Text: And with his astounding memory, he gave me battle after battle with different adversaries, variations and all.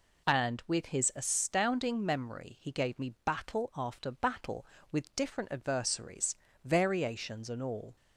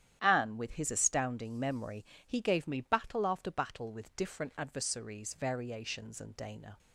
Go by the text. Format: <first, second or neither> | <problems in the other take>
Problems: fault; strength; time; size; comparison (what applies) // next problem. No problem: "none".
first | starts louder than the rest; strong; until 1.2 s; 10.5 dB // says "dana" for "all"; at 6.3 s